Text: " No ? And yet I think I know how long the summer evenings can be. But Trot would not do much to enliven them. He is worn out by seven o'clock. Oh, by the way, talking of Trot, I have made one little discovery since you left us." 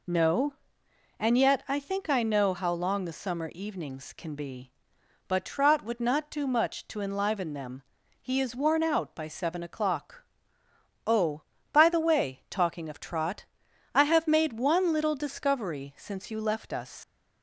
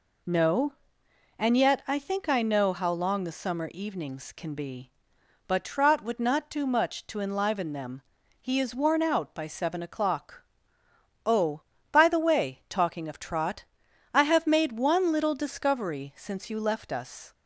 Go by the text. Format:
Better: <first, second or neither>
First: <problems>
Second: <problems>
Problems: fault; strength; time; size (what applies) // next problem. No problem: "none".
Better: second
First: leaves "us" unfinished; at 17.0 s; 110 ms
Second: none